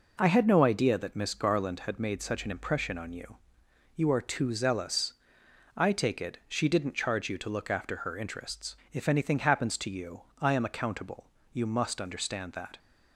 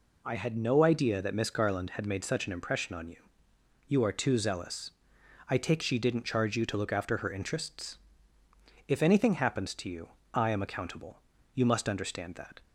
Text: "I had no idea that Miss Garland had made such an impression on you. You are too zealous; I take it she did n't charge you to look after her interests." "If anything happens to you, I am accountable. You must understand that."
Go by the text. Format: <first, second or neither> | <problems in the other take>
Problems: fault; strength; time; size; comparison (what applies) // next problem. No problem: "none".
first | skips "it"; at 5.8 s